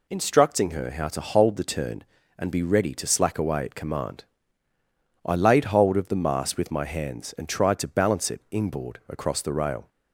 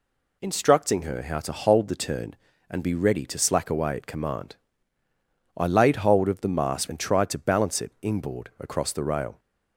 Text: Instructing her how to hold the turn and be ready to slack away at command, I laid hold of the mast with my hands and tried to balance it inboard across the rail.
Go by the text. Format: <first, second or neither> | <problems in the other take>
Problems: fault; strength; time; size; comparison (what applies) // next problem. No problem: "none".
first | skips "with my hands"; at 6.8 s